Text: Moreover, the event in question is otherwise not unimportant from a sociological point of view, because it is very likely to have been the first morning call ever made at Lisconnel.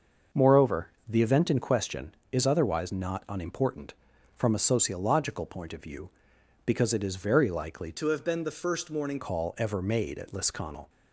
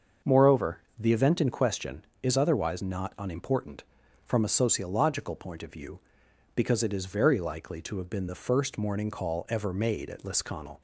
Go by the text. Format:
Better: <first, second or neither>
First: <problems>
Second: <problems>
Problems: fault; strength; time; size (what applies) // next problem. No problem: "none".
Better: second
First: starts louder than the rest; until 1.5 s; 6 dB // changes voice from "to" to "morning"; from 7.9 to 9.1 s; 1.2 s long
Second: starts louder than the rest; until 1.4 s; 6.5 dB